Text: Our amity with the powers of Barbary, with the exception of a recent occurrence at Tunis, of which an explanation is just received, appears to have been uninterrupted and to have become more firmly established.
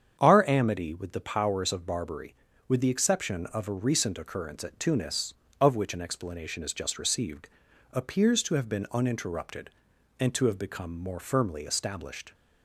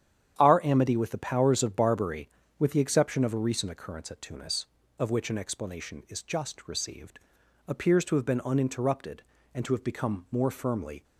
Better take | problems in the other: first | starts louder than the rest; strong; until 1.3 s; 9.5 dB; strong in the first // stops before "established"; at 11.0 s

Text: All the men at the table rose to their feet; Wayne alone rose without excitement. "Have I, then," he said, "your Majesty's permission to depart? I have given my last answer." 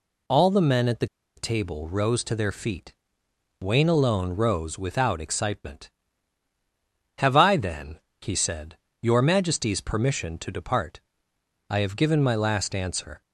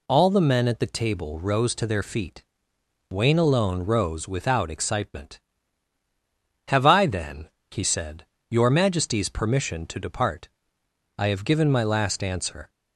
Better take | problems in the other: second | pauses between "the" and "table"; slight; at 1.0 s; 0.30 s long

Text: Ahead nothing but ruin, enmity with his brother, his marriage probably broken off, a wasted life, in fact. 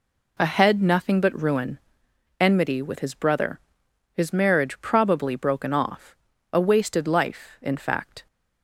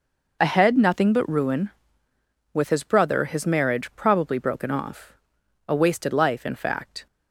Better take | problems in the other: first | skips "enmity"; at 2.1 s

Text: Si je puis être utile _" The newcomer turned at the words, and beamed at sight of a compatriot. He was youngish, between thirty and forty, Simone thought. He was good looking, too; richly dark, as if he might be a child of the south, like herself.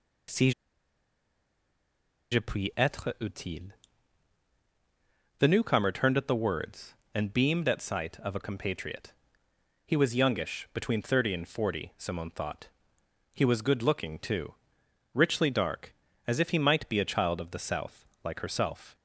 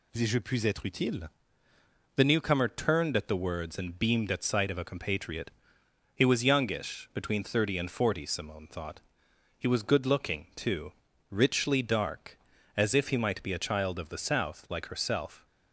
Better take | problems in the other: second | pauses between "Si" and "je"; strong; at 0.5 s; 1.8 s long

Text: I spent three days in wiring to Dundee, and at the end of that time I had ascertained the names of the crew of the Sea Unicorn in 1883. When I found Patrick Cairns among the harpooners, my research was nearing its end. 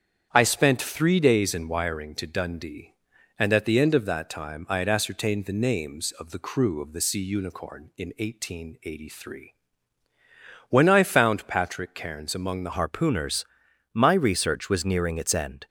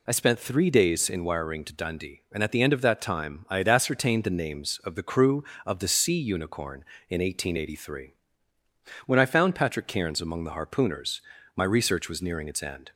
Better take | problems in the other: second | starts louder than the rest; strong; until 1.3 s; 8.5 dB // changes voice at "harpooners"; from 12.7 s on; 2.9 s long

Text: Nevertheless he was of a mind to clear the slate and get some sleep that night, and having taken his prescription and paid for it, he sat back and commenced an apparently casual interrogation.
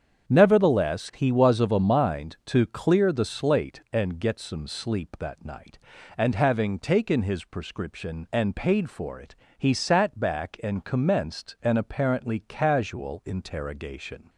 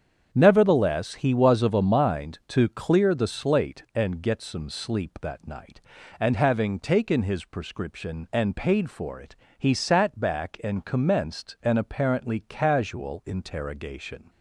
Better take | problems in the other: neither | starts louder than the rest; strong; the same in both

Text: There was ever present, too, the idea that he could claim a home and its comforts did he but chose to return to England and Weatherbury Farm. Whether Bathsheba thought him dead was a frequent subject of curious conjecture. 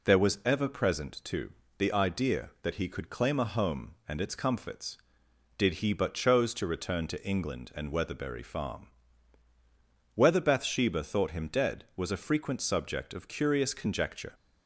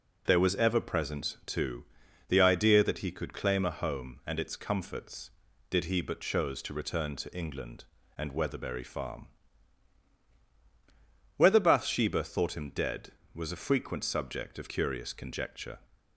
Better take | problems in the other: neither | none

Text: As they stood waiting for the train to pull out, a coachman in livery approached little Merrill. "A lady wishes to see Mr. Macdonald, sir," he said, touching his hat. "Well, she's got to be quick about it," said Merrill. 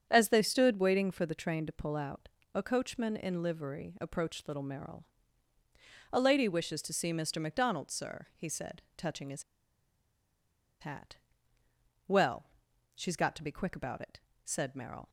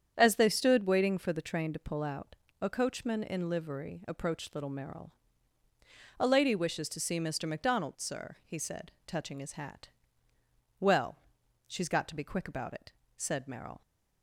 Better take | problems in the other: second | starts louder than the rest; strong; until 1.1 s; 8 dB; strong in the second // pauses between "his" and "hat"; strong; at 9.4 s; 1.3 s long

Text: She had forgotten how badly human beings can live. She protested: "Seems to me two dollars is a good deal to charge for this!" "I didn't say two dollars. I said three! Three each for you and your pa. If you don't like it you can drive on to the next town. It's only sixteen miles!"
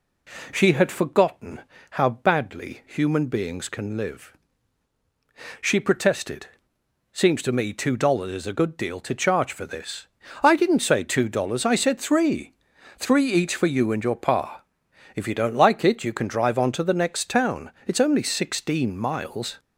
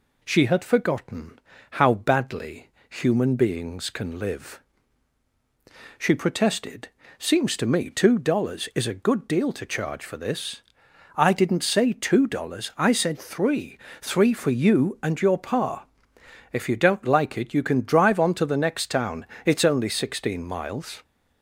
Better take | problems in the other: first | pauses between "forgotten" and "how"; slight; at 1.3 s; 0.32 s long; slight in the first // pauses between "badly" and "human"; slight; at 2.6 s; 0.20 s long // skips "each"; at 14.3 s

